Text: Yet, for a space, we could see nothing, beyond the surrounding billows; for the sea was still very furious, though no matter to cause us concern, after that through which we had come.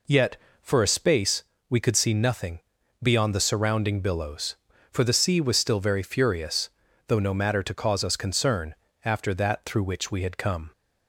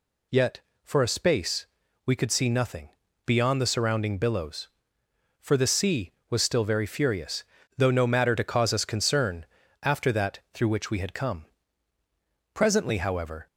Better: first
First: none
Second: goes on to say "Presently however"; noticeable; from 12.5 s on; 0.92 s long

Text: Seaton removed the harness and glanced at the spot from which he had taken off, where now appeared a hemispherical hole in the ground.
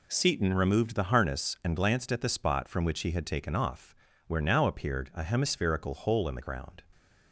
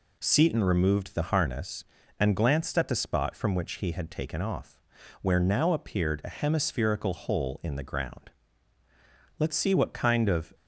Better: first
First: none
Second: goes on to say "Let's see what kind of"; noticeable; from 9.3 s on; 1.1 s long

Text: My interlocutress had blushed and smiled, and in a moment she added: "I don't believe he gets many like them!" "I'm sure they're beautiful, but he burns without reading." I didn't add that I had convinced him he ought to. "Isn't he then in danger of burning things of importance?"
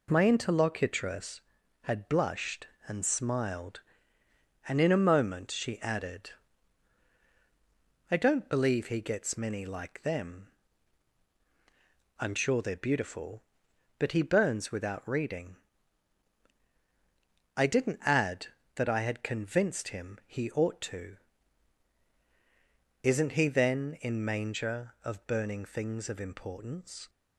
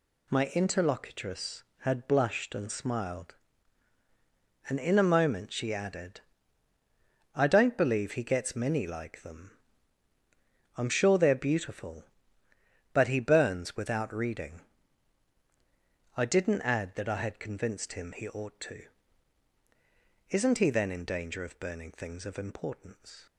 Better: second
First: says "manger" for "danger"; at 24.2 s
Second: none

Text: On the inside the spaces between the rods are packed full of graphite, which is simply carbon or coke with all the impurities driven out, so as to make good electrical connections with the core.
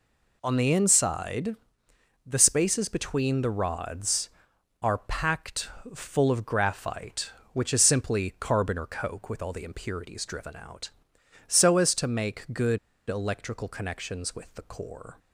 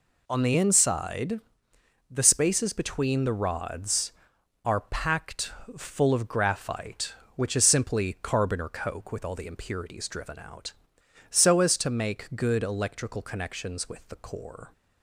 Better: second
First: pauses between "inside" and "the"; noticeable; at 1.5 s; 0.70 s long // pauses between "packed" and "full"; slight; at 5.6 s; 0.28 s long // pauses between "good" and "electrical"; slight; at 12.7 s; 0.29 s long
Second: pauses between "inside" and "the"; noticeable; at 1.3 s; 0.70 s long // pauses between "packed" and "full"; slight; at 5.4 s; 0.28 s long

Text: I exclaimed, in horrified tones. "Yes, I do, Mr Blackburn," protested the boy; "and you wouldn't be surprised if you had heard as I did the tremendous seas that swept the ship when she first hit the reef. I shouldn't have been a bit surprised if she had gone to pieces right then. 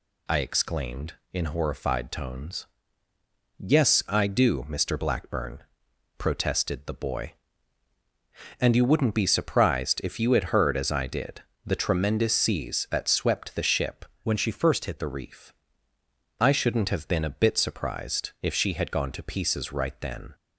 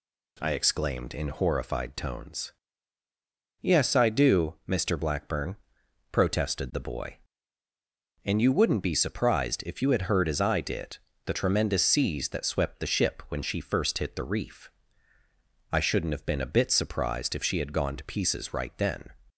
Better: second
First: pauses between "did" and "the"; slight; at 11.4 s; 0.22 s long // changes voice from "when" to "hit"; from 14.2 to 14.9 s; 0.7 s long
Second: pauses between "did" and "the"; slight; at 10.9 s; 0.28 s long

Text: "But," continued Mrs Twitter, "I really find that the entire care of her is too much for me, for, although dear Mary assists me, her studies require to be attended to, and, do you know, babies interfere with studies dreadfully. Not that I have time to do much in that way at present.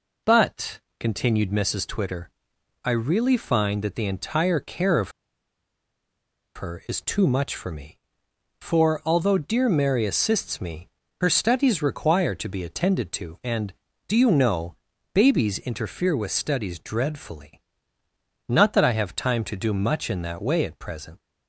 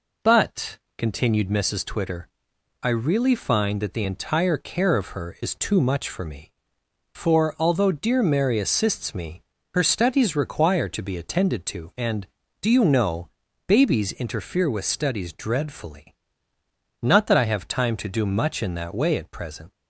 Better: second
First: pauses between "of" and "her"; strong; at 5.1 s; 1.4 s long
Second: none

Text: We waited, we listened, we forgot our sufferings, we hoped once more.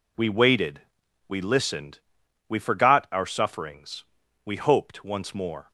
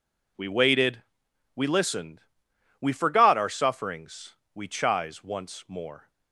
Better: first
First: none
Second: says "chise" for "hoped"; at 4.6 s

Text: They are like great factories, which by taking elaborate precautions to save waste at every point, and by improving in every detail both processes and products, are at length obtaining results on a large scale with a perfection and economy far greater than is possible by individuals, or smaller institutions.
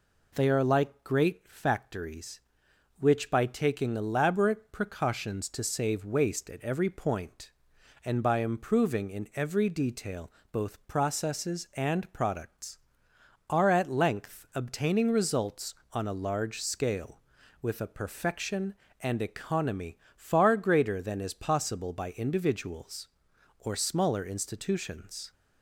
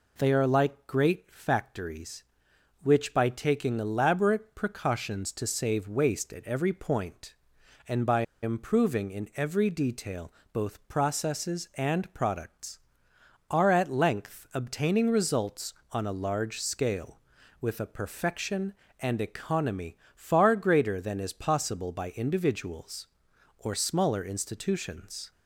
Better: first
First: pauses between "detail" and "both"; slight; at 10.3 s; 0.20 s long // pauses between "economy" and "far"; slight; at 19.9 s; 0.18 s long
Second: pauses between "by" and "improving"; slight; at 8.2 s; 0.19 s long // pauses between "detail" and "both"; slight; at 10.3 s; 0.20 s long // pauses between "economy" and "far"; slight; at 19.9 s; 0.18 s long

